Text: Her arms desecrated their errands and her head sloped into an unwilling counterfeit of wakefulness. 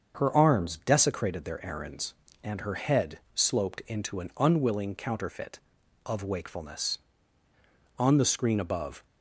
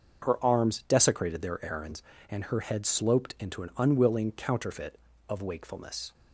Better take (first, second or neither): second